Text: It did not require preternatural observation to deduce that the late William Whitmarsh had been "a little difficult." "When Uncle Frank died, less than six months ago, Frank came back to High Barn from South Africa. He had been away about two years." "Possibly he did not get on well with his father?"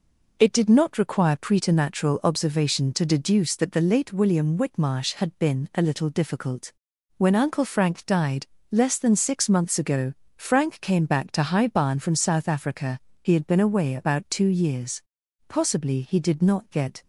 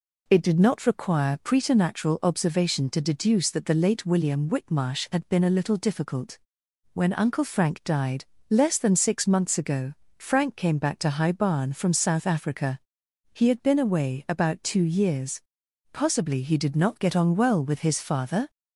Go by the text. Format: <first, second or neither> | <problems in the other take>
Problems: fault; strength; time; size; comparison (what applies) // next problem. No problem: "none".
second | stops before "on well with his father"; at 17.0 s